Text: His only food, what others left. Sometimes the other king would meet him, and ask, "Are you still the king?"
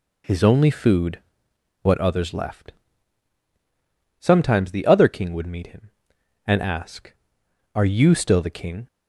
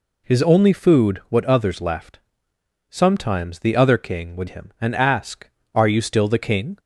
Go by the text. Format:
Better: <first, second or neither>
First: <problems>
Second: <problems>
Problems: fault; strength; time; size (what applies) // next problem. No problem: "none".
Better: first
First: none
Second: skips "meet"; at 4.4 s